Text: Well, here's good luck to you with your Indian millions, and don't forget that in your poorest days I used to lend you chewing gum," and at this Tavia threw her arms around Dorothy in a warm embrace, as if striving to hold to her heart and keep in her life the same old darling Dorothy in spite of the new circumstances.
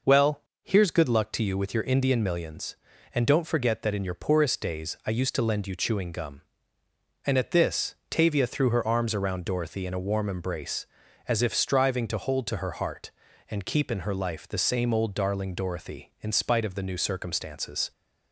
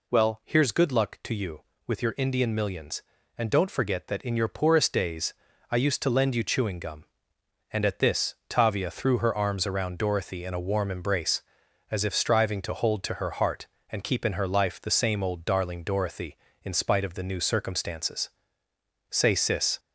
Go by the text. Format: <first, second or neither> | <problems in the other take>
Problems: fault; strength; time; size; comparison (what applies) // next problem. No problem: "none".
first | pauses between "days" and "I"; slight; at 5.3 s; 0.36 s long // goes on to say "Say Sis"; noticeable; from 19.0 s on; 0.70 s long